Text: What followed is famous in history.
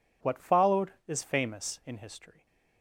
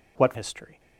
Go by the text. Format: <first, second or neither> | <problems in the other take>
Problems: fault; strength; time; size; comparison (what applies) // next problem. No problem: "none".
first | skips "followed is famous in"; at 0.3 s